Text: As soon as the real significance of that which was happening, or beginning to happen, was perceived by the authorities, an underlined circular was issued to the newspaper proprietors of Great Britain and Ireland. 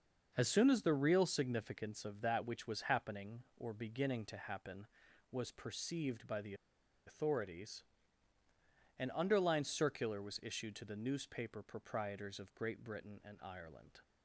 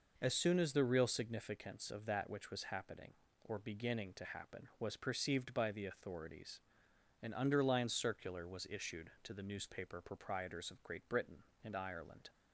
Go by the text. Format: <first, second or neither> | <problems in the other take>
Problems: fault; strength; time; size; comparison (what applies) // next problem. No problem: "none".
second | starts louder than the rest; until 1.3 s; 6 dB // pauses between "the" and "authorities"; noticeable; at 6.5 s; 0.52 s long